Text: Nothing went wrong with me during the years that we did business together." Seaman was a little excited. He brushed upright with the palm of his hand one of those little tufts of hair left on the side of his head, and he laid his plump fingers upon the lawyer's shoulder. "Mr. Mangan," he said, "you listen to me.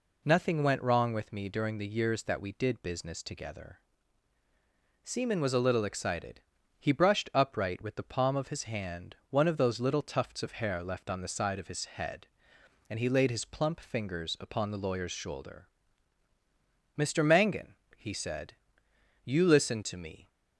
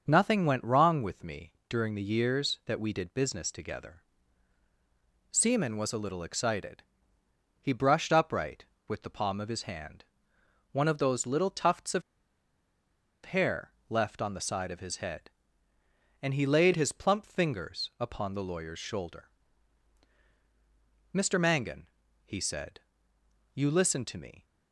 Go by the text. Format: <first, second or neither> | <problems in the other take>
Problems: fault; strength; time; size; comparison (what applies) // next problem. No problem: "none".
first | starts louder than the rest; until 1.0 s; 6.5 dB // pauses between "me" and "during"; slight; at 1.5 s; 0.18 s long // pauses between "hand" and "one"; noticeable; at 10.0 s; 0.68 s long; slight in the first // pauses between "of" and "hair"; at 12.0 s; 1.2 s long // pauses between "hair" and "left"; slight; at 13.7 s; 0.18 s long